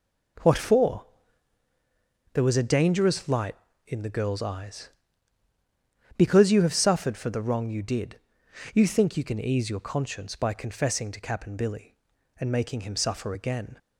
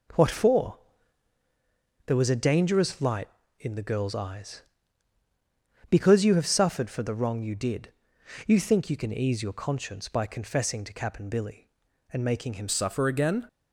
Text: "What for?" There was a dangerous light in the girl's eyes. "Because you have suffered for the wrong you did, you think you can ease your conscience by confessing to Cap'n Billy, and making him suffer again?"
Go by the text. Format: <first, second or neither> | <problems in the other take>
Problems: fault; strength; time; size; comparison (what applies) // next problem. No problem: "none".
first | changes voice at "suffer"; from 12.6 s on; 0.8 s long